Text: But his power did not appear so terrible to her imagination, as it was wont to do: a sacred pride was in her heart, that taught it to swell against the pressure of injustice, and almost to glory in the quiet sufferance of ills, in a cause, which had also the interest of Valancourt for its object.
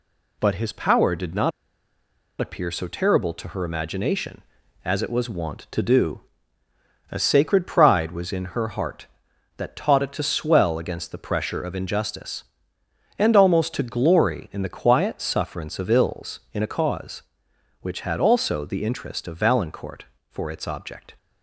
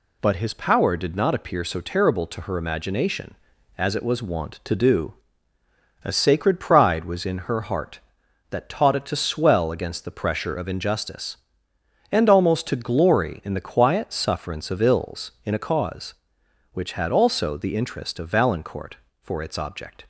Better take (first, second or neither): second